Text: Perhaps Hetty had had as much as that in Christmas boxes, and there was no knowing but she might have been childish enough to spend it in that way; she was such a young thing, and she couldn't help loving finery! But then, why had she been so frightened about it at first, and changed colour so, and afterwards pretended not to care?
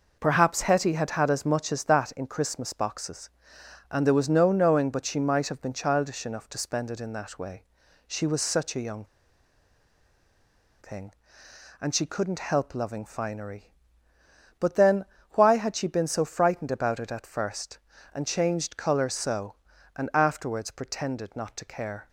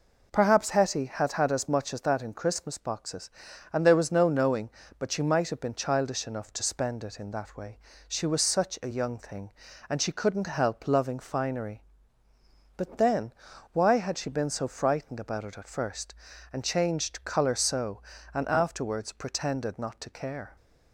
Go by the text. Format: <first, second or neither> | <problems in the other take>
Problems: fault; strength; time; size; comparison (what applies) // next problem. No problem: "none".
second | pauses between "young" and "thing"; strong; at 9.0 s; 1.7 s long